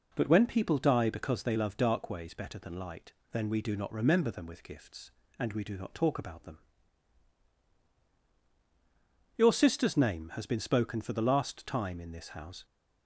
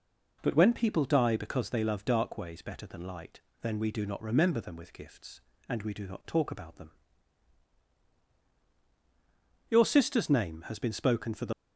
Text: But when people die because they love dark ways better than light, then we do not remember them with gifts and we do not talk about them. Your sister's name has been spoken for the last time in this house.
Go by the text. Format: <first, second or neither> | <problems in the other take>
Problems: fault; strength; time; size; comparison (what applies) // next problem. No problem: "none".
first | stops before "last time in this house"; at 11.5 s